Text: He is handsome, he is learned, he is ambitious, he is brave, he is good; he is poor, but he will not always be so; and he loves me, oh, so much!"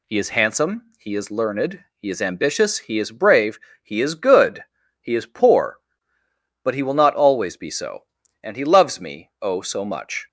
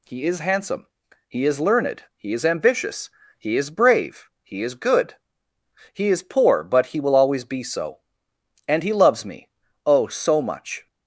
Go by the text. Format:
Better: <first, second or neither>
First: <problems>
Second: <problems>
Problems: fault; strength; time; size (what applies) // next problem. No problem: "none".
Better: first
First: none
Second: skips "not"; at 7.1 s